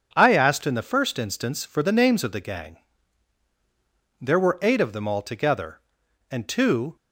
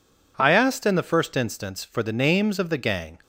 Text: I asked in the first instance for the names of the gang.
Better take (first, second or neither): second